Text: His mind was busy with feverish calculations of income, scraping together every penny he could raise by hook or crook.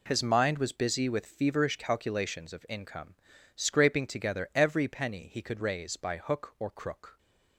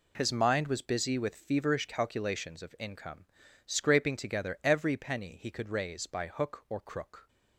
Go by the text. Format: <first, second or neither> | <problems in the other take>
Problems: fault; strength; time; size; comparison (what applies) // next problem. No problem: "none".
neither | none